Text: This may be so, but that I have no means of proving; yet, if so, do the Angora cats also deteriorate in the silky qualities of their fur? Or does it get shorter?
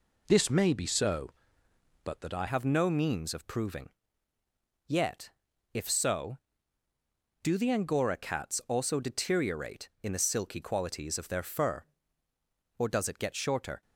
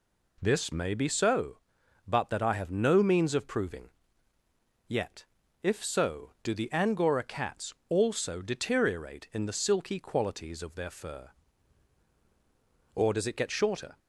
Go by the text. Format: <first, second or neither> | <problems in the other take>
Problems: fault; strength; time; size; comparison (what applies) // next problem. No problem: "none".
second | changes voice at "have"; from 2.4 s on; 11.4 s long